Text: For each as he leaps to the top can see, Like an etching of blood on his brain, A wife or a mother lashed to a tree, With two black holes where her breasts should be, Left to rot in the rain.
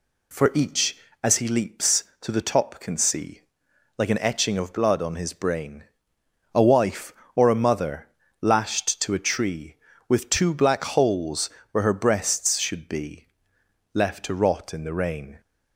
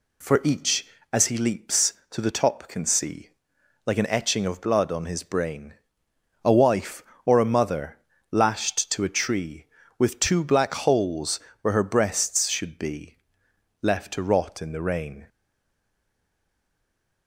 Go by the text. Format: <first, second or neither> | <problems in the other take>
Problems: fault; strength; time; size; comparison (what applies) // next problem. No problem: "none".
first | pauses between "mother" and "lashed"; slight; at 7.9 s; 0.34 s long; slight in the first // pauses between "holes" and "where"; slight; at 11.4 s; 0.22 s long; slight in the first // stays silent after the last word; noticeable; from 15.2 s on; 2.0 s long